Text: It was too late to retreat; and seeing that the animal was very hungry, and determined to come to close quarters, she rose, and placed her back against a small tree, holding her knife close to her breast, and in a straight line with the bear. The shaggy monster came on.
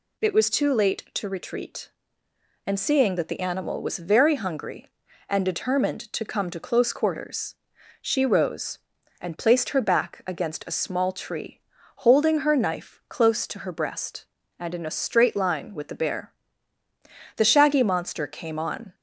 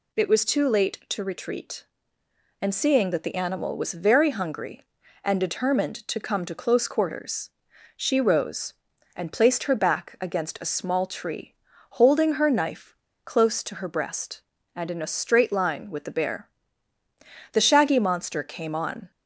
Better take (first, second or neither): first